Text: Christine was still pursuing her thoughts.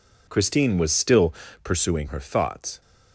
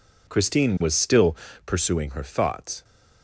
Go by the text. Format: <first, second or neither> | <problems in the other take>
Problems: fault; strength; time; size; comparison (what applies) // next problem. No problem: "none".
neither | pauses between "still" and "pursuing"; slight; the same in both